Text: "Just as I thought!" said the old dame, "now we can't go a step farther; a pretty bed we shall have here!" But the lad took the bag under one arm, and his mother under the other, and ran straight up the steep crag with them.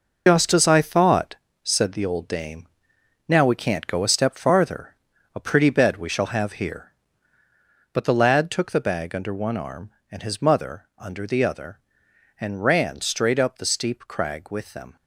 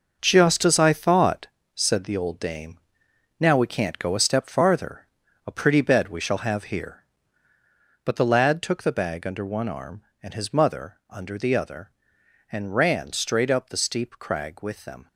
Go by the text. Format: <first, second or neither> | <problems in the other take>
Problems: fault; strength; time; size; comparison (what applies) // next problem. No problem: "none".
second | loses the start of "Just"; at 0.2 s; 165 ms